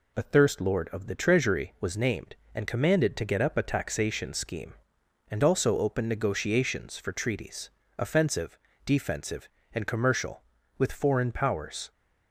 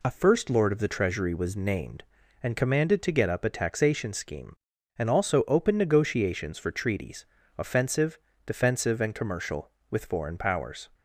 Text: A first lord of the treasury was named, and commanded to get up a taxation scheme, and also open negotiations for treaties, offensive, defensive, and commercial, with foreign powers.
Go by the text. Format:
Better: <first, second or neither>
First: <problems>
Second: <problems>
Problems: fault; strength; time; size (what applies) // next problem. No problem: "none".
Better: second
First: says "thirst" for "first"; at 0.2 s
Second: none